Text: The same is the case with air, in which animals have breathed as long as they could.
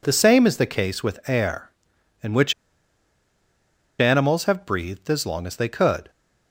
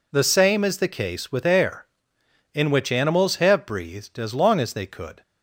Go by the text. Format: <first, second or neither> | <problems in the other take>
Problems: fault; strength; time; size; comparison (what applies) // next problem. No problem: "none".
second | pauses between "which" and "animals"; strong; at 2.5 s; 1.4 s long